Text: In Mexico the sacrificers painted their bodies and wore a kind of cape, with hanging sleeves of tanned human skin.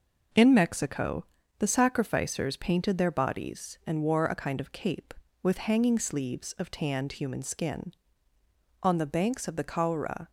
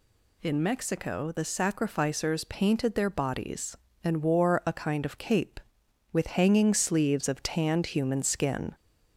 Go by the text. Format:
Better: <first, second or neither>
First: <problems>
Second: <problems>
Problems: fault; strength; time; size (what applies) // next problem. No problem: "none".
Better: second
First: pauses between "Mexico" and "the"; slight; at 1.2 s; 0.34 s long // goes on to say "On the banks of the Caura"; from 8.8 s on; 1.4 s long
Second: none